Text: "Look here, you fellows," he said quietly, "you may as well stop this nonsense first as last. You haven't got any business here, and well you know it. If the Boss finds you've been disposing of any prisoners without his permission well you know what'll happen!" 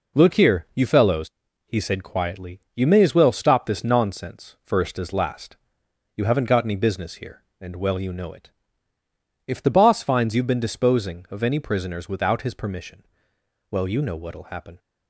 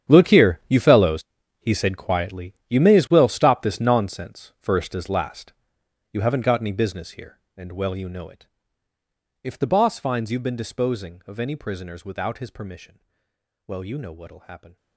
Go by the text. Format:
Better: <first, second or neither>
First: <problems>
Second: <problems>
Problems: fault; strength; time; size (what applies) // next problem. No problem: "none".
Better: first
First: pauses between "permission" and "well"; noticeable; at 13.0 s; 0.68 s long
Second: gets quieter; strong; throughout; 16 dB // pauses between "permission" and "well"; noticeable; at 12.9 s; 0.68 s long